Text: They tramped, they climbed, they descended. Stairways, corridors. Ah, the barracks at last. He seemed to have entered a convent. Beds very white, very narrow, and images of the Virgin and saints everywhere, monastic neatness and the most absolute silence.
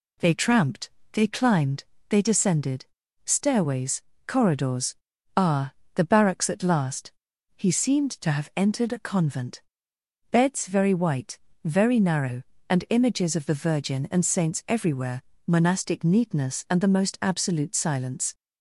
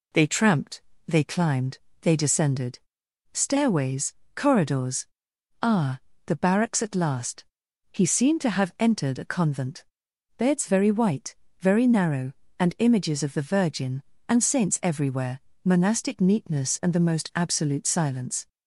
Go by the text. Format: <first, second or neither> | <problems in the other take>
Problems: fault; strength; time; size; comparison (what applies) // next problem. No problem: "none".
neither | none